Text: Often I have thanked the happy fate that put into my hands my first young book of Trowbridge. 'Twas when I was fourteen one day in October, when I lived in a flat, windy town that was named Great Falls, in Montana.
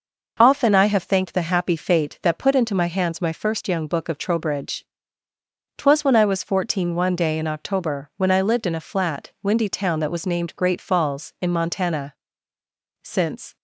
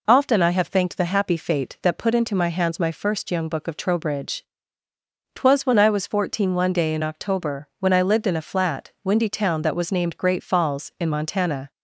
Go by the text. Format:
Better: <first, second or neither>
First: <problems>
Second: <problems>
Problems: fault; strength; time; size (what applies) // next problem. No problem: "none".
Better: second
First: goes on to say "Since"; from 13.0 s on; 0.54 s long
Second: none